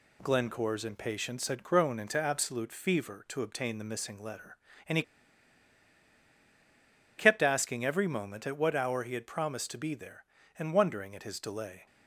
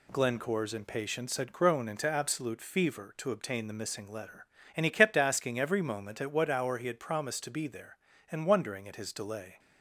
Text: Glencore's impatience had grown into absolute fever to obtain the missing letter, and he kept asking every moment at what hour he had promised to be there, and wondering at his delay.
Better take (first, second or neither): second